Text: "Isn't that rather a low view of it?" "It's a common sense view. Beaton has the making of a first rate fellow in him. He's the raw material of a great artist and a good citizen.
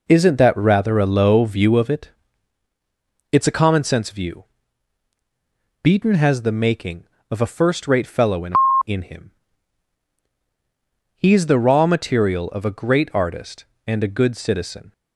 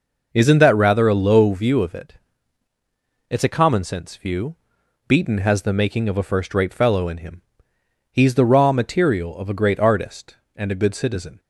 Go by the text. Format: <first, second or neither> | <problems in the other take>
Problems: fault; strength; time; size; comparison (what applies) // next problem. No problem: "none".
second | says "in" twice; at 8.8 s